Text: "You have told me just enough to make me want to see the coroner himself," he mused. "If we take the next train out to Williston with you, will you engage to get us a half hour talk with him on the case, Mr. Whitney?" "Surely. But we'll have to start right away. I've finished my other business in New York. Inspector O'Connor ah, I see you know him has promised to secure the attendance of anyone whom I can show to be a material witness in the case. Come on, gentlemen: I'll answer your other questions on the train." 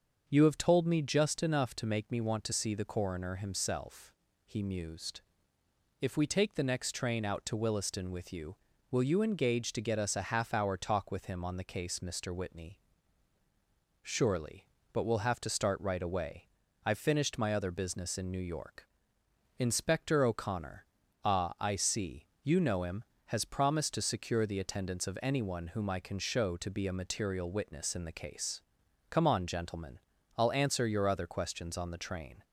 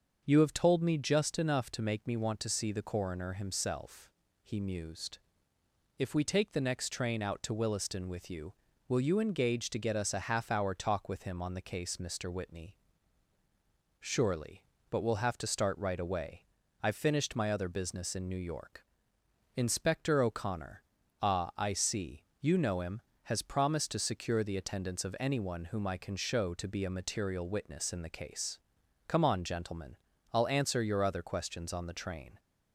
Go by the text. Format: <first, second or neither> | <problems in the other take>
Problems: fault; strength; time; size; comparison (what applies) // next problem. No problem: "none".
neither | starts louder than the rest; the same in both // pauses between "O'Connor" and "ah"; the same in both // pauses between "see" and "you"; slight; the same in both